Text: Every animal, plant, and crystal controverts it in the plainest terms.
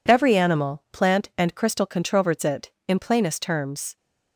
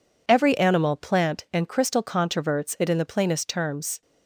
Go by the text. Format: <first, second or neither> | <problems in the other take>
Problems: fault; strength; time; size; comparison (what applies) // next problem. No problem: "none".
second | skips "the"; at 2.9 s